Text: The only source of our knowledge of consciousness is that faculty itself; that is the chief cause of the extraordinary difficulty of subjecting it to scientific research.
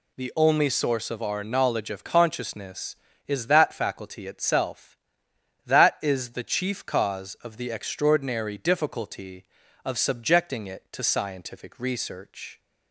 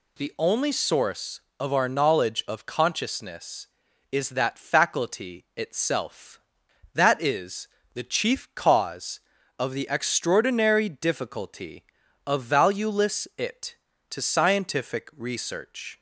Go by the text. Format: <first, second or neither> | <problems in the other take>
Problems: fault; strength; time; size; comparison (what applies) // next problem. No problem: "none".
first | pauses between "is" and "the"; slight; at 7.6 s; 0.26 s long // says "valueless" for "subjecting"; at 12.4 s